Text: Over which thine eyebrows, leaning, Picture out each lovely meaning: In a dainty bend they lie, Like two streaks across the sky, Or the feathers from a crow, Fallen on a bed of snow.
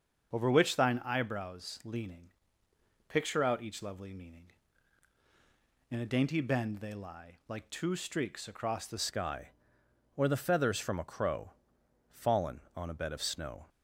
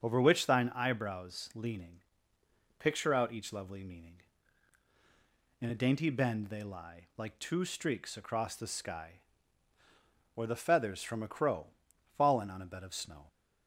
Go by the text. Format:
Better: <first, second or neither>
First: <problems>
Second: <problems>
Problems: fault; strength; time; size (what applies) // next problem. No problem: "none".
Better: second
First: starts louder than the rest; until 1.3 s; 6.5 dB // changes voice at "sky"; from 8.9 s on; 4.7 s long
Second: starts louder than the rest; until 1.0 s; 7 dB